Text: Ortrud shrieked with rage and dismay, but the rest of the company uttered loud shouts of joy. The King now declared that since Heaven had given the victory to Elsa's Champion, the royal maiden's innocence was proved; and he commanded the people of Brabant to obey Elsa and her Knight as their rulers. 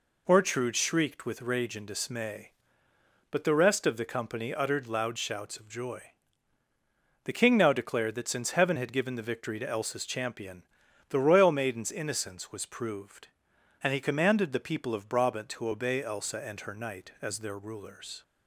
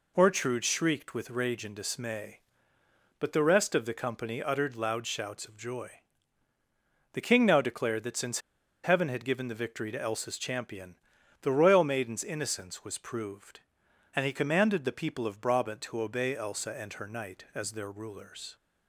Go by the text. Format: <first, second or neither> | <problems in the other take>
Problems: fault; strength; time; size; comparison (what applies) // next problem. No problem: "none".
first | pauses between "since" and "Heaven"; at 8.4 s; 0.42 s long